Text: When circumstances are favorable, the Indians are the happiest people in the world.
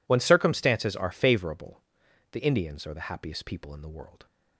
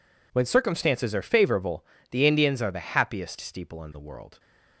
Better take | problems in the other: first | says "steeple" for "people"; at 3.3 s

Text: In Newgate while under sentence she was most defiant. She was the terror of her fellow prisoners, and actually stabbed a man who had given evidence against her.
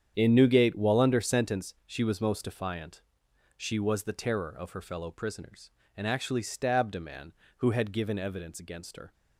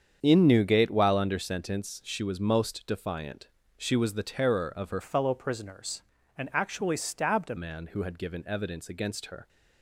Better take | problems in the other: first | starts louder than the rest; strong; until 1.2 s; 7.5 dB; strong in the first // changes voice from "fellow" to "a"; from 5.0 to 7.5 s; 2.5 s long

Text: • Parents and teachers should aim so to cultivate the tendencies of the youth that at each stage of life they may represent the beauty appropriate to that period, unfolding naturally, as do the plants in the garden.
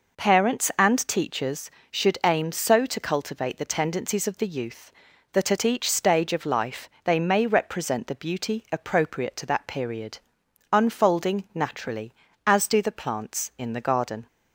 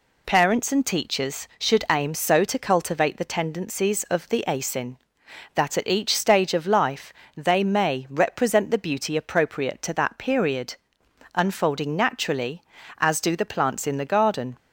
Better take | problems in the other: first | says "asin" for "youth"; at 4.4 s // pauses between "life" and "they"; slight; at 7.1 s; 0.24 s long

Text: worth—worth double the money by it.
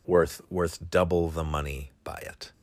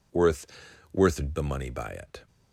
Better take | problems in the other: first | skips "double"; at 1.3 s

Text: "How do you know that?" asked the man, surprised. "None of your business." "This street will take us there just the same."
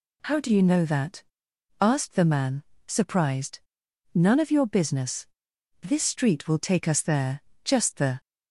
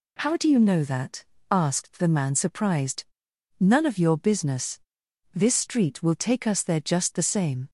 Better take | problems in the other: second | pauses between "there" and "just"; slight; at 7.4 s; 0.22 s long // stops before "same"; at 8.1 s

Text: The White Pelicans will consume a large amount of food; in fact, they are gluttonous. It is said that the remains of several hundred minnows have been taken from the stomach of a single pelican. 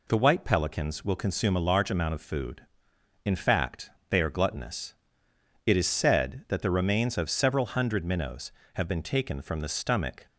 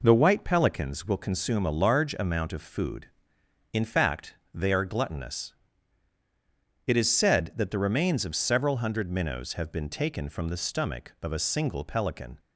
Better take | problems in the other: second | stops before "of a single pelican"; at 10.2 s

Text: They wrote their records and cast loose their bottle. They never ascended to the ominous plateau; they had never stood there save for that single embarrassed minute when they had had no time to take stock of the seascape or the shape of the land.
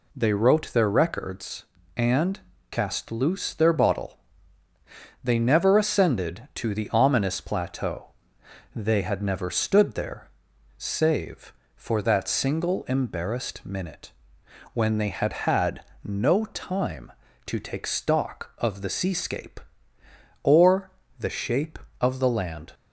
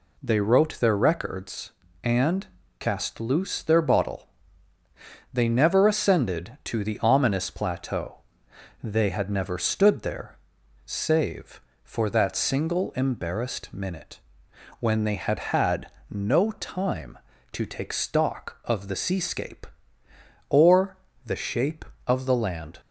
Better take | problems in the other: neither | pauses between "and" and "cast"; slight; the same in both // pauses between "there" and "save"; noticeable; the same in both // pauses between "minute" and "when"; noticeable; the same in both // pauses between "had" and "no"; slight; the same in both // pauses between "or" and "the"; slight; the same in both

